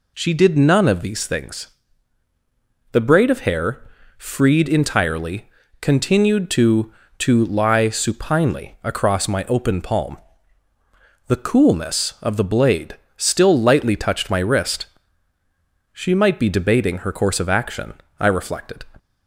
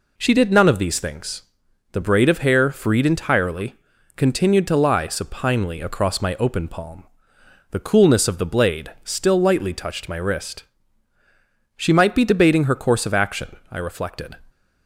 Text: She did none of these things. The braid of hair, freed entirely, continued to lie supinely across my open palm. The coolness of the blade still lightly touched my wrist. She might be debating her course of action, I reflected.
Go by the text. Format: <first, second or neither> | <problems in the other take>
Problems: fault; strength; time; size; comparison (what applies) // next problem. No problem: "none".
second | says "to" twice; at 7.1 s // pauses between "blade" and "still"; slight; at 12.9 s; 0.20 s long